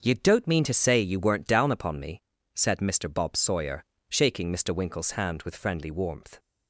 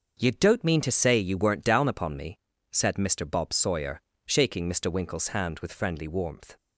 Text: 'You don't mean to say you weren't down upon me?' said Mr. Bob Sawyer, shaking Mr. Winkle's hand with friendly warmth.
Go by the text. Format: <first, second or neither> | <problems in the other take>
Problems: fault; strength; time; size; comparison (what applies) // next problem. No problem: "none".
neither | starts louder than the rest; noticeable; the same in both